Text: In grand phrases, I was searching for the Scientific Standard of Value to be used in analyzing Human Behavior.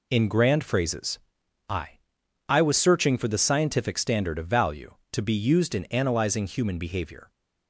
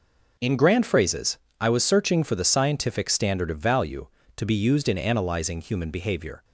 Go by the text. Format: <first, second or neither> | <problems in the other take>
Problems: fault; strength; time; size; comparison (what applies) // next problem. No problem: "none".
second | says "I" twice; at 2.4 s